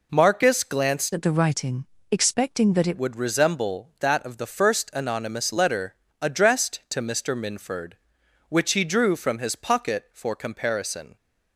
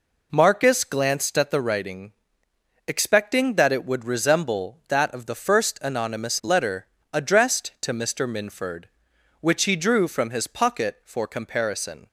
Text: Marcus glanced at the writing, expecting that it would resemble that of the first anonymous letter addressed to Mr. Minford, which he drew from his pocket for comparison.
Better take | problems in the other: second | changes voice from "at" to "it"; from 1.1 to 2.9 s; 1.8 s long // pauses between "letter" and "addressed"; slight; at 5.9 s; 0.26 s long; slight in the second

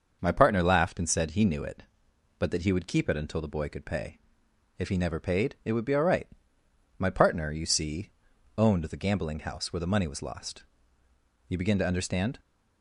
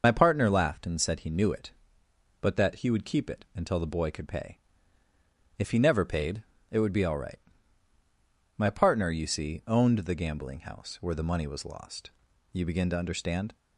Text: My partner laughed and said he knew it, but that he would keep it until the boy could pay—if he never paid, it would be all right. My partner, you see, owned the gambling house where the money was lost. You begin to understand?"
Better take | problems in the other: first | loses the start of "My"; at 0.0 s; 35 ms // starts louder than the rest; noticeable; until 1.0 s; 6 dB; also in the first

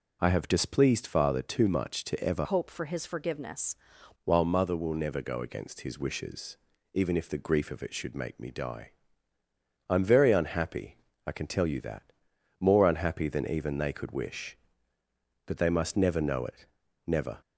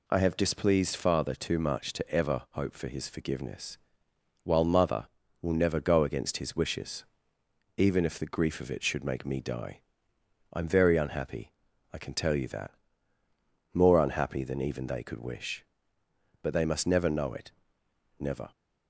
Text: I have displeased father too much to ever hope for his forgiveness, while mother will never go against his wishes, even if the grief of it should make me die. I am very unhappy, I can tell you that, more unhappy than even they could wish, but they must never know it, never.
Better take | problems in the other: second | changes voice from "hope" to "forgiveness"; from 2.4 to 3.7 s; 1.3 s long

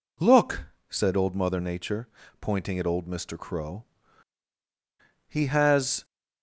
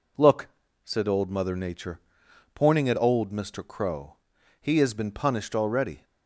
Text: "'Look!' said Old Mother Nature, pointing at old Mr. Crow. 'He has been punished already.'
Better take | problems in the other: second | stops before "been punished already"; at 6.0 s

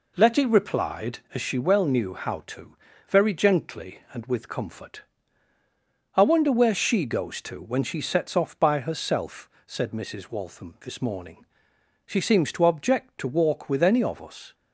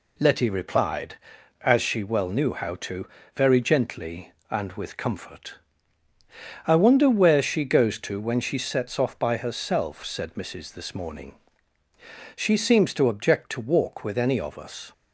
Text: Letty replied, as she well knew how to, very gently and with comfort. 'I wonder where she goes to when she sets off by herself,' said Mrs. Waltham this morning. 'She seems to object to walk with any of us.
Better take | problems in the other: first | skips "Waltham"; at 10.7 s

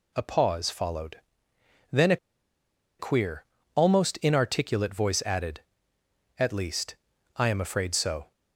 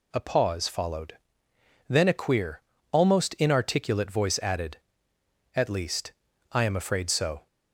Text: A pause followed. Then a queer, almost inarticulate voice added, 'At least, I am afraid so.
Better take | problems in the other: second | pauses between "a" and "queer"; noticeable; at 2.1 s; 0.82 s long

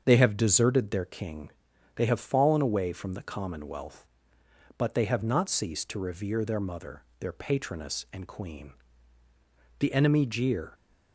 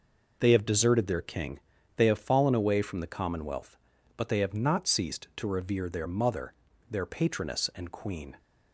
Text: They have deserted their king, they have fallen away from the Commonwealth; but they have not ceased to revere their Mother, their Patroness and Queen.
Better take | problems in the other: second | starts louder than the rest; until 1.0 s; 7 dB // goes on to say "The enemy jeer"; noticeable; from 9.7 s on; 0.94 s long

